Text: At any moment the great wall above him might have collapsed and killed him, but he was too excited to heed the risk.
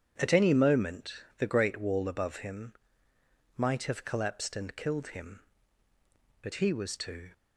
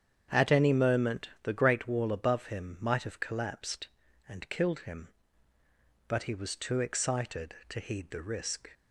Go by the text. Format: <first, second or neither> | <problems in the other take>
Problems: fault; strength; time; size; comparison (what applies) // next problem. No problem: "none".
second | starts louder than the rest; strong; until 1.4 s; 9 dB; strong in the second // pauses between "moment" and "the"; slight; at 1.1 s; 0.24 s long // pauses between "him" and "might"; noticeable; at 2.7 s; 0.82 s long // stops before "excited to heed the risk"; at 7.3 s